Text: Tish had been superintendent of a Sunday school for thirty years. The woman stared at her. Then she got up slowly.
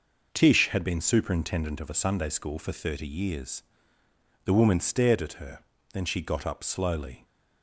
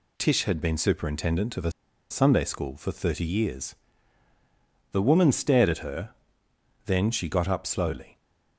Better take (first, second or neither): first